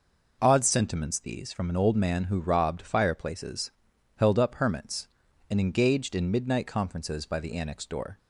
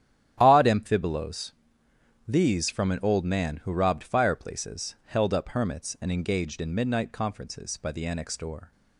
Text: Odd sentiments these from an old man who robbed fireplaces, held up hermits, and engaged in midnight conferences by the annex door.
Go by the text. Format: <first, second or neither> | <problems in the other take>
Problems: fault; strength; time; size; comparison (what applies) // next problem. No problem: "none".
first | starts louder than the rest; strong; until 1.4 s; 11.5 dB // says "amphibolos" for "sentiments"; at 0.6 s